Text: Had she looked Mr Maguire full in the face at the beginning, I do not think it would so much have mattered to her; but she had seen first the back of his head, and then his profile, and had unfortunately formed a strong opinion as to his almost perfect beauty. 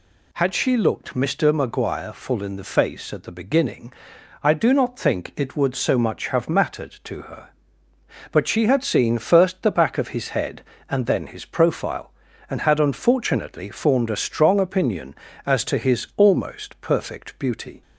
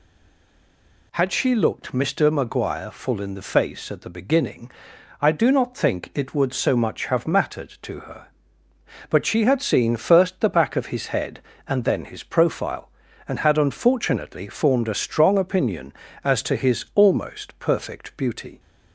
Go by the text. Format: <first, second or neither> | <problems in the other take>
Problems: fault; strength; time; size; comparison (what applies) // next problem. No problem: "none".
first | stays silent before the first word; until 1.1 s; 1.1 s long